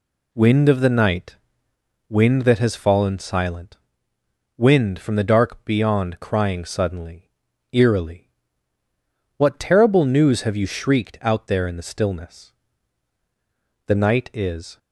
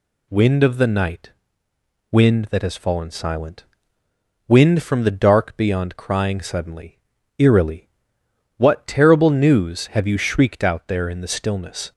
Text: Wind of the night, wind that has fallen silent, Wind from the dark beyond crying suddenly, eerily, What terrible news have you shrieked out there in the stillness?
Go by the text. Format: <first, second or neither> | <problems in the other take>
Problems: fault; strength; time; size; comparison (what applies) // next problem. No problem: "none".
second | goes on to say "The night is"; noticeable; from 13.8 s on; 0.90 s long